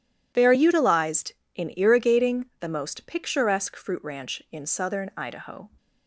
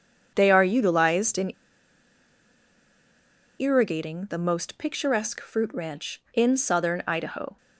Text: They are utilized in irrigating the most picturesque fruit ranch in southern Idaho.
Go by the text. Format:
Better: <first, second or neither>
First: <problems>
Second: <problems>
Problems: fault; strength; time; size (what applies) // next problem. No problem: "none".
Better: first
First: none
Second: pauses between "in" and "irrigating"; strong; at 1.5 s; 2.0 s long